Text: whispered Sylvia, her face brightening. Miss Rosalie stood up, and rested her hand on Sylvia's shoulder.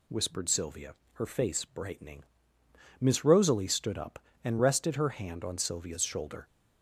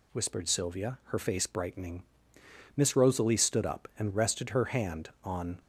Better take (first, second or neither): first